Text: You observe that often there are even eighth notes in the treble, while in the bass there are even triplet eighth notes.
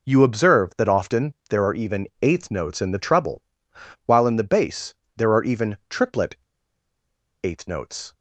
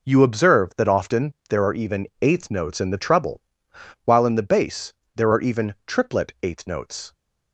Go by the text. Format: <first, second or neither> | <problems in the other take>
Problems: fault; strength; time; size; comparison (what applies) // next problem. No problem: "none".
second | pauses between "bass" and "there"; slight; at 4.9 s; 0.22 s long; slight in the second // pauses between "triplet" and "eighth"; at 6.3 s; 1.0 s long